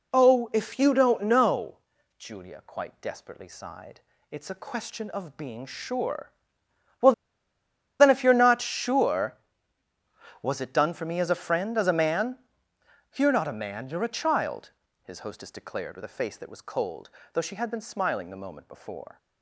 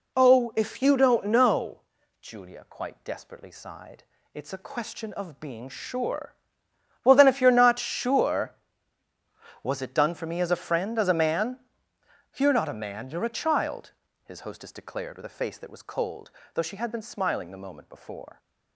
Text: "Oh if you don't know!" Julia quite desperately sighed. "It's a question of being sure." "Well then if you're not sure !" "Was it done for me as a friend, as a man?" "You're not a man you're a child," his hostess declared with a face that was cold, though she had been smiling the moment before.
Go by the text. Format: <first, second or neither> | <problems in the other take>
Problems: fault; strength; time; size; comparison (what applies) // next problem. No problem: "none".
second | pauses between "Well" and "then"; noticeable; at 7.1 s; 0.87 s long